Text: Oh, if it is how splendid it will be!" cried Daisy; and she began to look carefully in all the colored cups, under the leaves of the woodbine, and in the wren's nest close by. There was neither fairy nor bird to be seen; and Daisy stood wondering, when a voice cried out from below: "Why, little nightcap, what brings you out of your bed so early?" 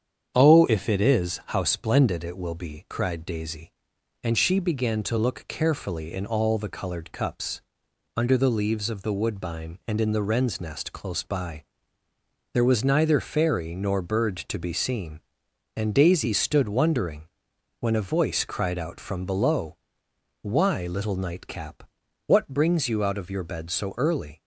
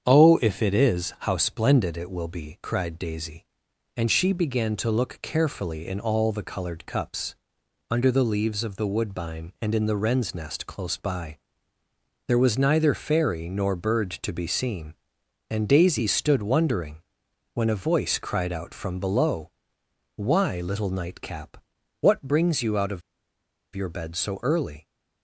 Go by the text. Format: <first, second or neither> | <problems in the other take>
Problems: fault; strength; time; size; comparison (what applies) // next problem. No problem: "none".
first | starts louder than the rest; strong; until 1.0 s; 7.5 dB; strong in the first // pauses between "of" and "your"; noticeable; at 23.0 s; 0.74 s long